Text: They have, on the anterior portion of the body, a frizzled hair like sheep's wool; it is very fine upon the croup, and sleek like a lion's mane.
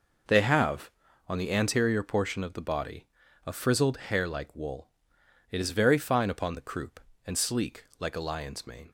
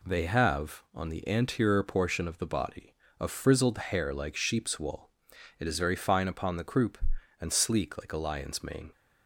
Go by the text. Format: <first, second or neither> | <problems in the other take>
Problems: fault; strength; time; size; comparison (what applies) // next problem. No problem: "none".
second | skips "sheep's"; at 4.5 s